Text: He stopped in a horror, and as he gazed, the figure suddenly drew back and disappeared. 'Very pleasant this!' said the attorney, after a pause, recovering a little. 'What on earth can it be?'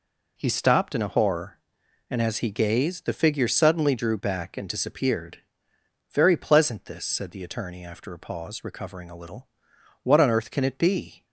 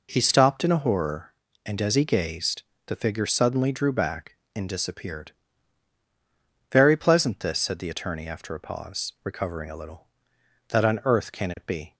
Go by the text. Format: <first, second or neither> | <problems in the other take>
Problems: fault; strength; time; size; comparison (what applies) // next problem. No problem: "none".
first | says "That" for "What"; at 10.6 s